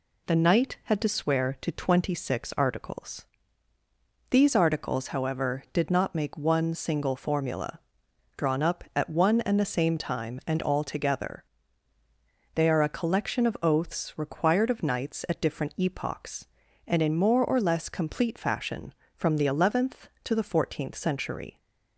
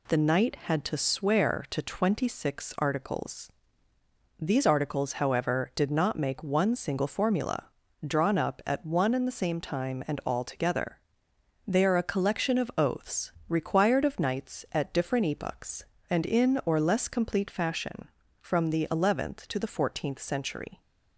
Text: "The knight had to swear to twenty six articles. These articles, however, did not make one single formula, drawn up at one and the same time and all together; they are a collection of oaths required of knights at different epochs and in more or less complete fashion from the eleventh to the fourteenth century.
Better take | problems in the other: first | pauses between "oaths" and "required"; slight; at 13.3 s; 0.16 s long // skips "more"; at 16.6 s

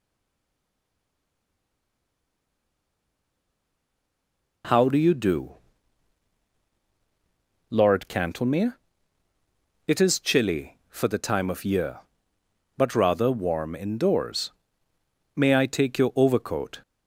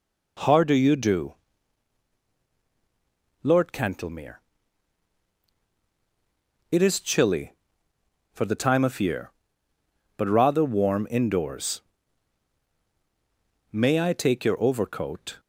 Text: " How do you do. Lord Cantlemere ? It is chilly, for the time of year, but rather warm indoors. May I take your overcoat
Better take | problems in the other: second | stays silent before the first word; strong; until 4.6 s; 4.6 s long

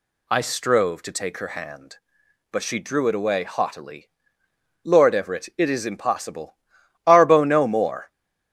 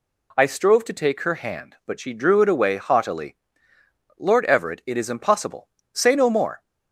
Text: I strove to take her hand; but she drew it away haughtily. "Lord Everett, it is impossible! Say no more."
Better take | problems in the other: second | says "Arbo" for "Say"; at 7.0 s

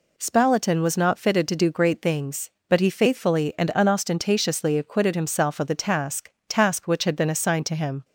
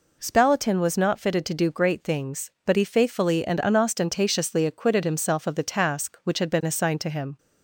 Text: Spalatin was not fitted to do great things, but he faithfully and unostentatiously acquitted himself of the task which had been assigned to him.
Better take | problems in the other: second | says "task" twice; at 6.4 s

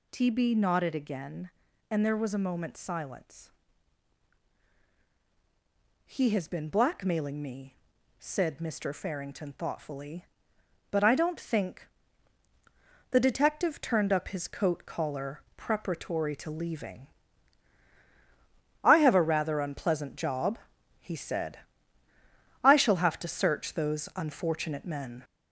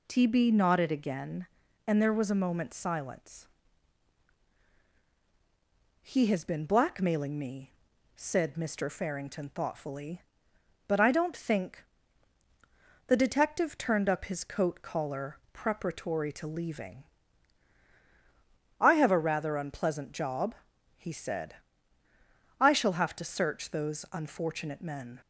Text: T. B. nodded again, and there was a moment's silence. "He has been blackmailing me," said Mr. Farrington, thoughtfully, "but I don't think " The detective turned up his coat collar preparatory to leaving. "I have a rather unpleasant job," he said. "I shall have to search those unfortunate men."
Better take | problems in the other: second | gets louder; noticeable; throughout; 4.5 dB // pauses between "collar" and "preparatory"; slight; at 15.4 s; 0.16 s long; slight in the second

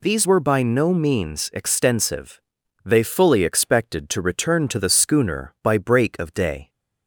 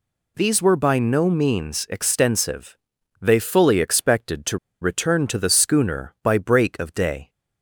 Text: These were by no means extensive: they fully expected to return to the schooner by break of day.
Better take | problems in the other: first | pauses between "to" and "return"; slight; at 4.5 s; 0.22 s long

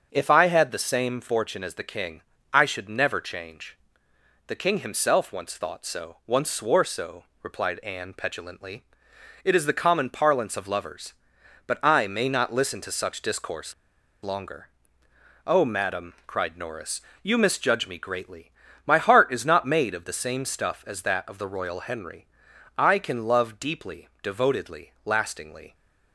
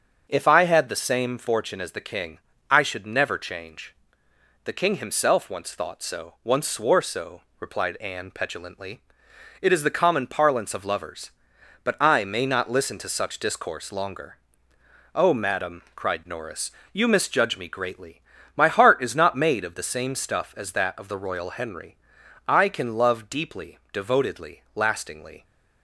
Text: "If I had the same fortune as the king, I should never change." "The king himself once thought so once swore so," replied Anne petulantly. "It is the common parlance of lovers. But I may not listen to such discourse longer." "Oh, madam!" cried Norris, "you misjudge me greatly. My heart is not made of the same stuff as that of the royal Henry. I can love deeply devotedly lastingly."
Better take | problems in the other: second | starts louder than the rest; until 1.1 s; 6.5 dB; also in the second // pauses between "discourse" and "longer"; noticeable; at 13.7 s; 0.49 s long

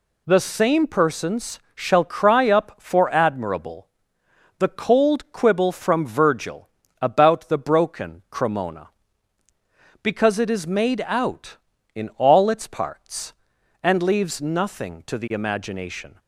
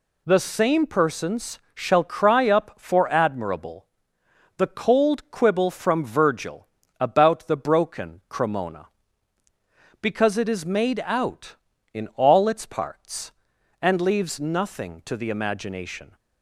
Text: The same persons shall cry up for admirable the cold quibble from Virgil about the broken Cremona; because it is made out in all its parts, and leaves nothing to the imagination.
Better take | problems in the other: neither | pauses between "persons" and "shall"; slight; the same in both // pauses between "admirable" and "the"; noticeable; the same in both // pauses between "Virgil" and "about"; slight; the same in both

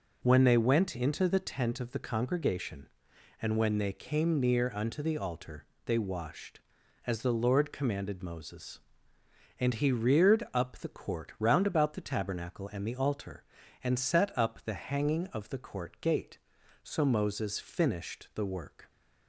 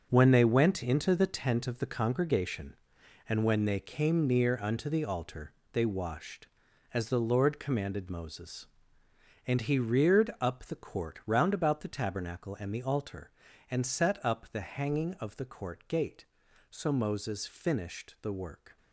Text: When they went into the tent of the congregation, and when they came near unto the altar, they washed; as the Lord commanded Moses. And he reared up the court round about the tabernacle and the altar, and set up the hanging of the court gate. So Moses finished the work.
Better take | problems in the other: first | gets quieter; strong; throughout; 10 dB

